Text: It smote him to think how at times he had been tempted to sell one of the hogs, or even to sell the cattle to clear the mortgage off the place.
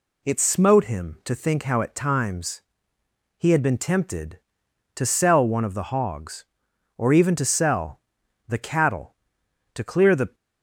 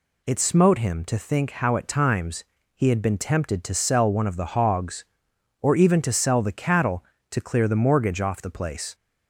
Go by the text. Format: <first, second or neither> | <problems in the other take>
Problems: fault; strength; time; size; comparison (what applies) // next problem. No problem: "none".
second | pauses between "times" and "he"; noticeable; at 2.6 s; 0.74 s long; slight in the second // pauses between "sell" and "the"; noticeable; at 8.0 s; 0.48 s long // stops before "mortgage off the place"; at 10.3 s